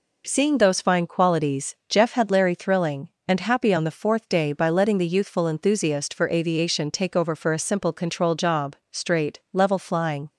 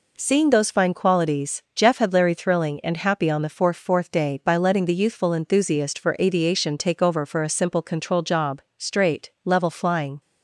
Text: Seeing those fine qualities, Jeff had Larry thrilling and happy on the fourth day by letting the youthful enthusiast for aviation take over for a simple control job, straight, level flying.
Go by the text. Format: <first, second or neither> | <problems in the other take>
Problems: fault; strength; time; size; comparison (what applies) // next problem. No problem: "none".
first | says "fourth" twice; at 3.7 s